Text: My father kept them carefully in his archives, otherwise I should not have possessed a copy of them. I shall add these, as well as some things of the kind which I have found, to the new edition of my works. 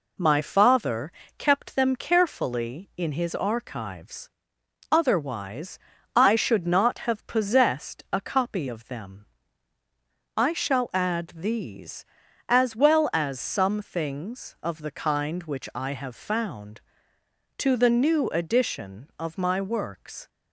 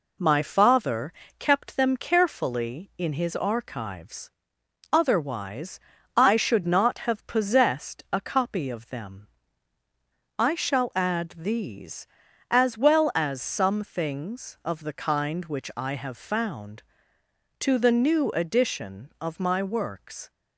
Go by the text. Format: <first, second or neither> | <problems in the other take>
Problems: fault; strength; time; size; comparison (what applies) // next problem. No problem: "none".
neither | pauses between "father" and "kept"; slight; the same in both // pauses between "otherwise" and "I"; the same in both